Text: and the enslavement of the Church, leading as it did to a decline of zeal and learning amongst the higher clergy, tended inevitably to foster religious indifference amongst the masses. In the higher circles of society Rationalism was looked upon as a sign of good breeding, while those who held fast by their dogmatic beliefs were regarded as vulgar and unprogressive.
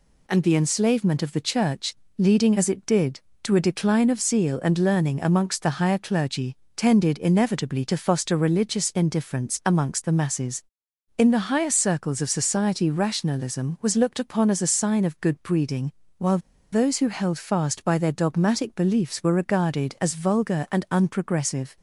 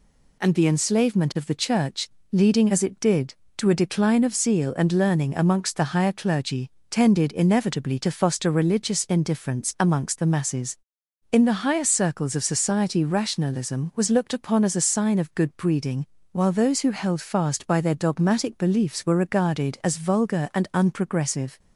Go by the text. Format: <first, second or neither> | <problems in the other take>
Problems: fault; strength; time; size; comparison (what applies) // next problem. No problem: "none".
second | pauses between "while" and "those"; slight; at 16.3 s; 0.33 s long